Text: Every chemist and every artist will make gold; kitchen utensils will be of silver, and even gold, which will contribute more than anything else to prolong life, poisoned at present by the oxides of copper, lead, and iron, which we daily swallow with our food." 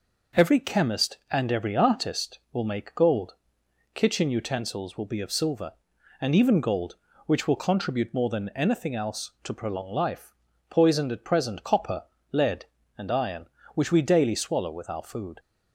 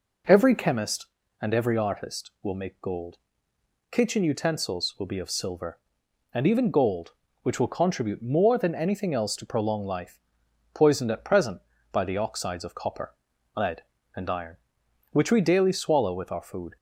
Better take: second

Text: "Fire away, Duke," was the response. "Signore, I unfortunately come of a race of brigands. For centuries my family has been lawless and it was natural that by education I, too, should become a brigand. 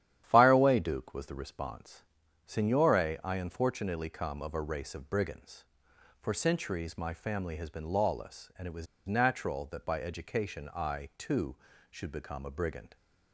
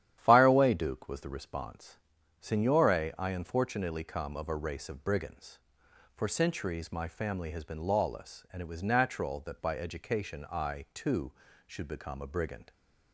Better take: second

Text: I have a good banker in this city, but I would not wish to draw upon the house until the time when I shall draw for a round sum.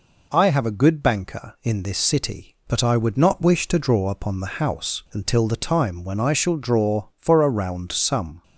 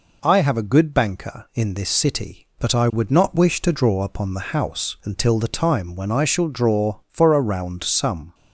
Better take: neither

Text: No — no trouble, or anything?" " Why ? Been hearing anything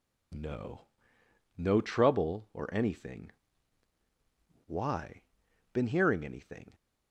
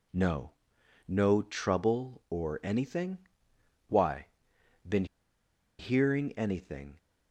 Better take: first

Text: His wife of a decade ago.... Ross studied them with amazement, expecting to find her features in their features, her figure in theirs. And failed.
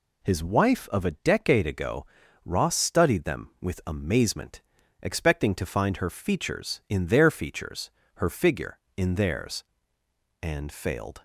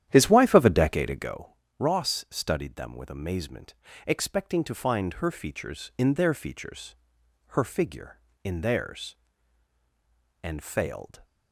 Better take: first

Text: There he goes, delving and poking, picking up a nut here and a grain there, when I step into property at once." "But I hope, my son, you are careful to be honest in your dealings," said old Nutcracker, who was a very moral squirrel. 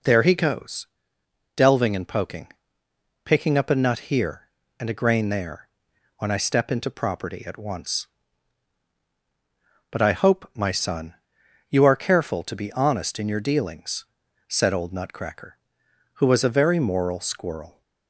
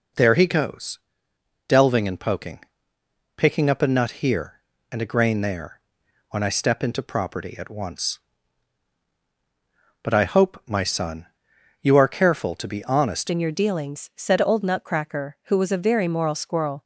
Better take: first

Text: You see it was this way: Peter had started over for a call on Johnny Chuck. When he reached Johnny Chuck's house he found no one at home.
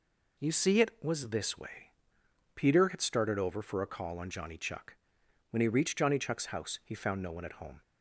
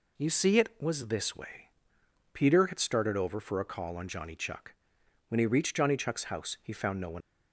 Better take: first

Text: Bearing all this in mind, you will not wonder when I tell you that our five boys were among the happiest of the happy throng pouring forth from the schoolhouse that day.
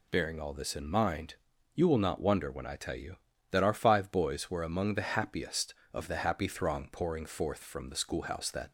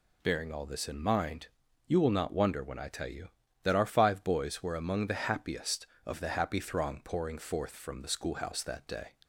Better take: second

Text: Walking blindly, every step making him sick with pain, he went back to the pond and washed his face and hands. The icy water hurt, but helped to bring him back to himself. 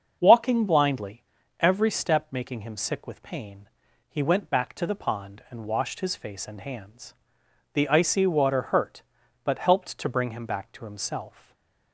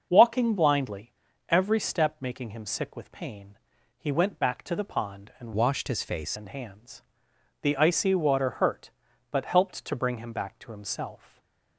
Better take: first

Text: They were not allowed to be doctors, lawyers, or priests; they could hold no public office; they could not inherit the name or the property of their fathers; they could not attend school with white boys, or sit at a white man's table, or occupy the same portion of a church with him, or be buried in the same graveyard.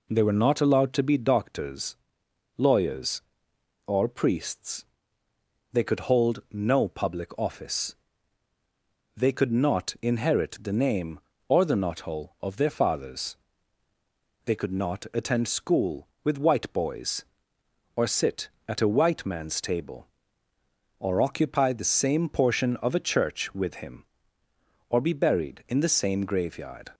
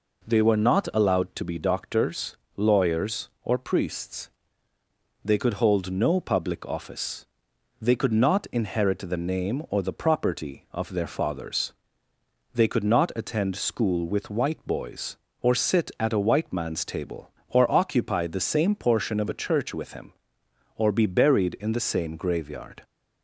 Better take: second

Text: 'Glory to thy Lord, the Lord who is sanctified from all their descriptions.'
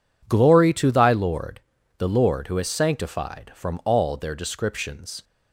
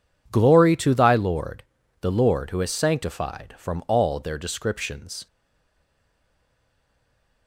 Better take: first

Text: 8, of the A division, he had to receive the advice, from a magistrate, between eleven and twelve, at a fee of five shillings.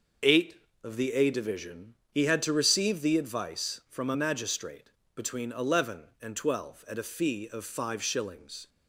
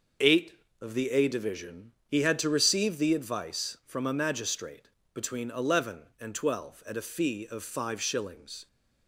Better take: neither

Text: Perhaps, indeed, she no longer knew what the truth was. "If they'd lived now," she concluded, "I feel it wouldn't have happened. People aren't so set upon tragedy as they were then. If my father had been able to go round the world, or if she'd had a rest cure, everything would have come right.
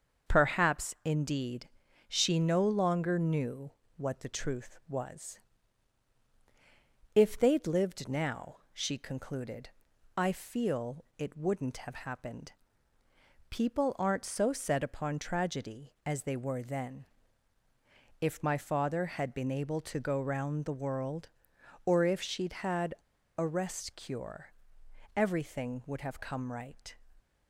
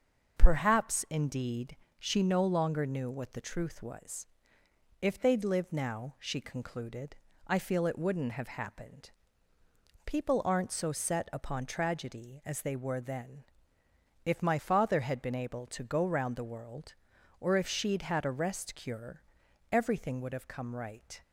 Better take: second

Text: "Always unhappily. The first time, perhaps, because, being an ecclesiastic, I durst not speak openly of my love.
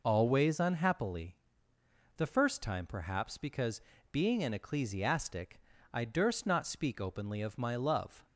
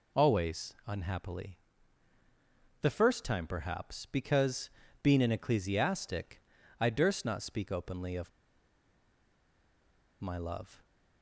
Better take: first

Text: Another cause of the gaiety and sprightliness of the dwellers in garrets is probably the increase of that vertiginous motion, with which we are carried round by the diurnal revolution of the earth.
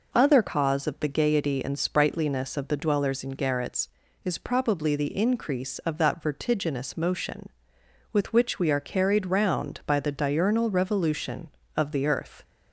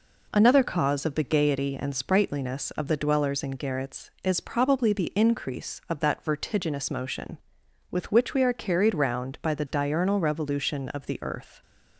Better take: second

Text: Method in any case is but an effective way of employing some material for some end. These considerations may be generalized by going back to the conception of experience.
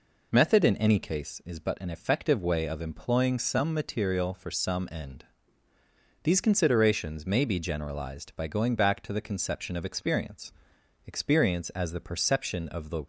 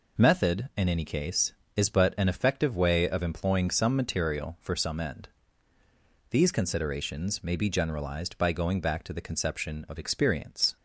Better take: second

